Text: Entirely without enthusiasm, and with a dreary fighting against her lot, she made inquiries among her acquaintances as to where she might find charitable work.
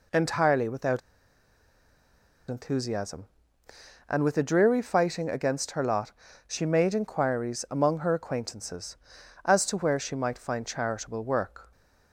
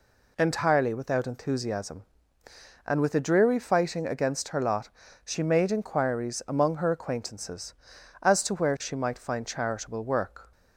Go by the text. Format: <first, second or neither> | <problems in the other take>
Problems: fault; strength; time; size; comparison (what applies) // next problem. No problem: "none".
second | pauses between "without" and "enthusiasm"; strong; at 1.0 s; 1.5 s long